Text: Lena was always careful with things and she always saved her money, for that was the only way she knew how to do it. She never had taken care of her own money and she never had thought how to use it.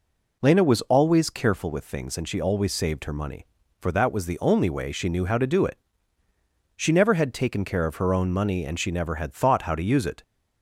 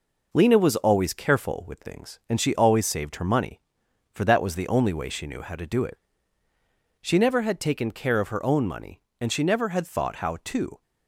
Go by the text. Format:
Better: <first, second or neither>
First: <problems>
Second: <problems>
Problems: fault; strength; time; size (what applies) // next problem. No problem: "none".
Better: first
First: none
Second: stops before "use it"; at 10.8 s